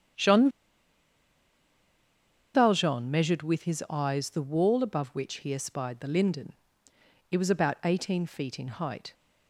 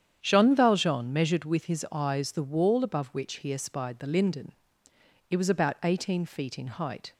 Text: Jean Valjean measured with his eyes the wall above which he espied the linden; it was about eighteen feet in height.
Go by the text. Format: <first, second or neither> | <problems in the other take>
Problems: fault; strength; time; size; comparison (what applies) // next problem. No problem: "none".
second | starts louder than the rest; strong; until 3.2 s; 9 dB; strong in the second // pauses between "Jean" and "Valjean"; strong; at 0.4 s; 2.0 s long